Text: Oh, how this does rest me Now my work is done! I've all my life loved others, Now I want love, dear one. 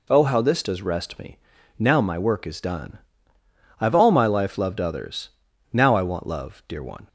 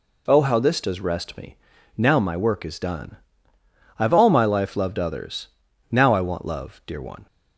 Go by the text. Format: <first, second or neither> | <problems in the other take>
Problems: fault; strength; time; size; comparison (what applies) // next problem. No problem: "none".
neither | pauses between "me" and "Now"; the same in both